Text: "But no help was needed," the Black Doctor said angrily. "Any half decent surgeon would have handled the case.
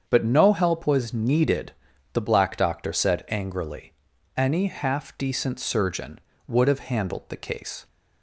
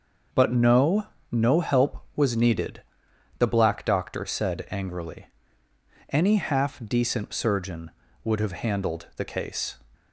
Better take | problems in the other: first | starts louder than the rest; until 1.5 s; 6 dB; strong in the first // says "no" twice; at 1.2 s

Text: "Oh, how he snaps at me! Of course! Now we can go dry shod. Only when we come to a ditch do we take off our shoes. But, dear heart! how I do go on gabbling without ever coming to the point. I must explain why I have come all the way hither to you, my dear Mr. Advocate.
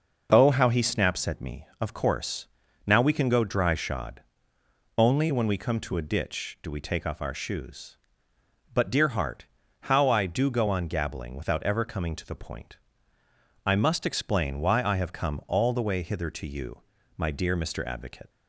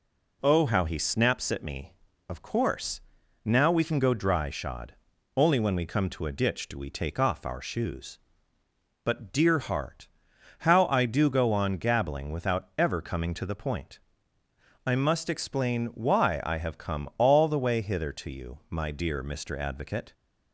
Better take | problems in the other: neither | none

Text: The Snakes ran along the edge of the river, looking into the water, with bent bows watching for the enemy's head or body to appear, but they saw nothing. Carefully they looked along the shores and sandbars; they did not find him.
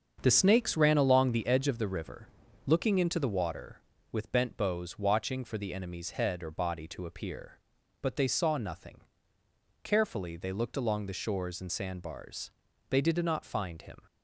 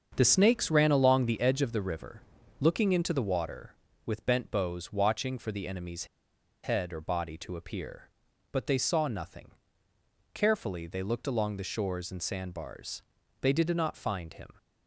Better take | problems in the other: first | starts louder than the rest; strong; until 1.1 s; 7 dB; strong in the first // pauses between "enemy's" and "head"; noticeable; at 6.0 s; 0.60 s long

